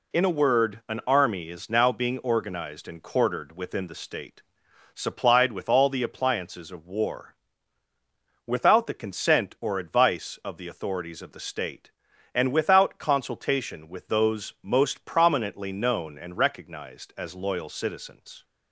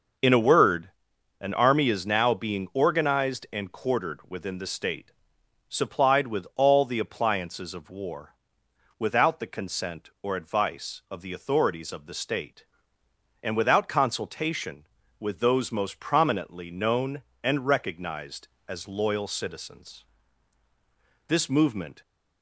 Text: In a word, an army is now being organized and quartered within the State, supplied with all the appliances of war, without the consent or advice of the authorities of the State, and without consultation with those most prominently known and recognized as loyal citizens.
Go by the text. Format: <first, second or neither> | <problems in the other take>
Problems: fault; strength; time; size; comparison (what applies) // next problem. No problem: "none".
first | goes on to say "This movement"; noticeable; from 21.2 s on; 0.74 s long